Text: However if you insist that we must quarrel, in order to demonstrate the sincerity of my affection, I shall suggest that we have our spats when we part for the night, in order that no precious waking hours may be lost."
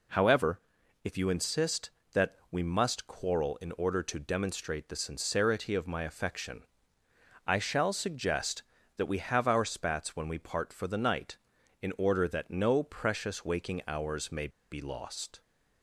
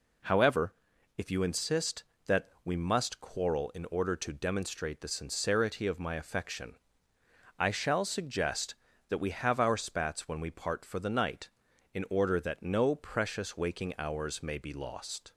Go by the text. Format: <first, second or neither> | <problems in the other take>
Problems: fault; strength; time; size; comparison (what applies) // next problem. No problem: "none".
second | pauses between "However" and "if"; at 0.6 s; 0.44 s long; also in the second // pauses between "that" and "we"; slight; at 2.3 s; 0.16 s long; slight in the second // pauses between "may" and "be"; slight; at 14.4 s; 0.21 s long